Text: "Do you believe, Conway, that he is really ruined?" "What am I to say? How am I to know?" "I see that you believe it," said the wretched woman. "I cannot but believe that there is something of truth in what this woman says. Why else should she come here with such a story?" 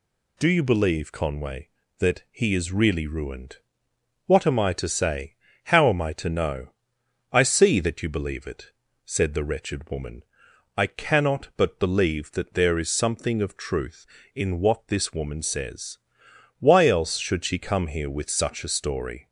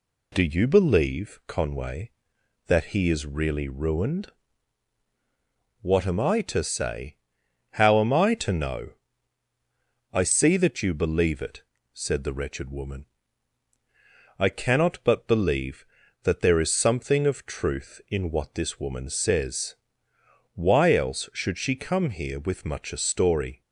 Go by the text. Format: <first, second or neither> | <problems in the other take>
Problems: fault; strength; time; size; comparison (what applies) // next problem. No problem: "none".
first | says "much" for "such"; at 22.6 s